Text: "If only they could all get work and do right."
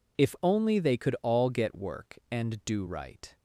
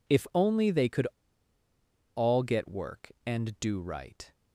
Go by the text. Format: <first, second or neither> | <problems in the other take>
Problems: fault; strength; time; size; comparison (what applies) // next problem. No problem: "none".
first | pauses between "could" and "all"; at 1.0 s; 1.0 s long